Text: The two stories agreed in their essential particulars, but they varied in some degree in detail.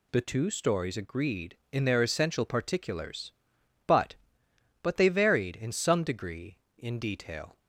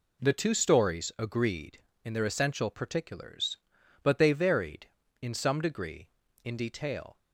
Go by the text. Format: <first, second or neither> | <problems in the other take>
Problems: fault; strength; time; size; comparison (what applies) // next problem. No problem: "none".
second | says "but" twice; at 4.8 s